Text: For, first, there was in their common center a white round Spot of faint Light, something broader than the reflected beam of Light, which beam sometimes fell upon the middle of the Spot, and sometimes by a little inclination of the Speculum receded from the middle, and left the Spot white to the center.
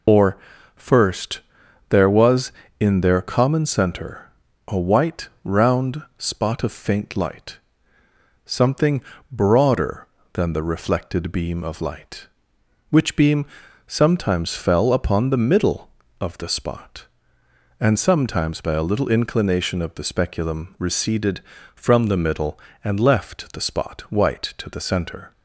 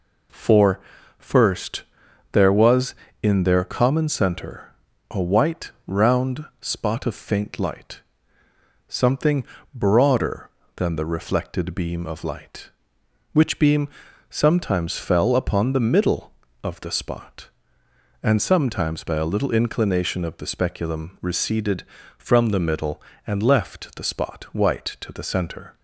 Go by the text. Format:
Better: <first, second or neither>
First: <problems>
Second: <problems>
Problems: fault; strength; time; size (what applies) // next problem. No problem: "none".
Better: second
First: loses the start of "For"; at 0.0 s; 195 ms // pauses between "center" and "a"; at 4.2 s; 0.40 s long // pauses between "white" and "round"; slight; at 5.2 s; 0.16 s long // pauses between "round" and "Spot"; slight; at 6.0 s; 0.16 s long // pauses between "something" and "broader"; slight; at 8.9 s; 0.32 s long // pauses between "beam" and "sometimes"; at 13.4 s; 0.40 s long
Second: pauses between "center" and "a"; at 4.7 s; 0.40 s long // pauses between "white" and "round"; slight; at 5.7 s; 0.16 s long // pauses between "round" and "Spot"; slight; at 6.4 s; 0.16 s long // pauses between "something" and "broader"; slight; at 9.4 s; 0.32 s long // pauses between "beam" and "sometimes"; at 13.8 s; 0.40 s long